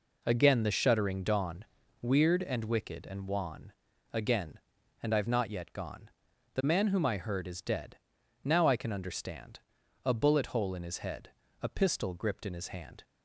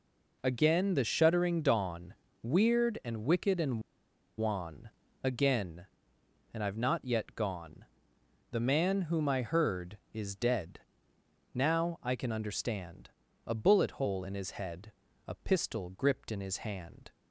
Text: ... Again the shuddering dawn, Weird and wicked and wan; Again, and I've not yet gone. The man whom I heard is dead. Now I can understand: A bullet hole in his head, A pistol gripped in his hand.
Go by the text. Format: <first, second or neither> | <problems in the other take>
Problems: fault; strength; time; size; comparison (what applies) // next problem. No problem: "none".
first | pauses between "and" and "wan"; noticeable; at 3.8 s; 0.56 s long